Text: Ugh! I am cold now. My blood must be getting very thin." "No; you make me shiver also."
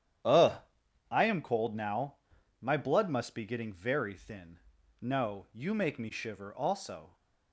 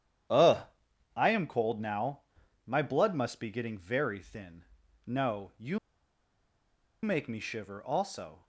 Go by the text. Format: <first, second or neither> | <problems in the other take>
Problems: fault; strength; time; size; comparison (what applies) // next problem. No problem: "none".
first | starts louder than the rest; strong; until 1.8 s; 10 dB; strong in the first // pauses between "you" and "make"; at 5.7 s; 1.2 s long